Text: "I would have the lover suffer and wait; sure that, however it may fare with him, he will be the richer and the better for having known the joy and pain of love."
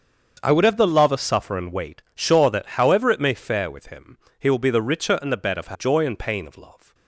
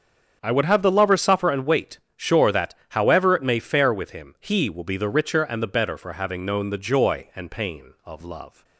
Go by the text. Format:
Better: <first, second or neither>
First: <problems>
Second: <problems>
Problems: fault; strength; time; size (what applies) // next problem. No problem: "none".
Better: second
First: starts louder than the rest; until 1.4 s; 7 dB // skips "having known the"; at 5.7 s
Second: starts louder than the rest; strong; until 1.4 s; 7 dB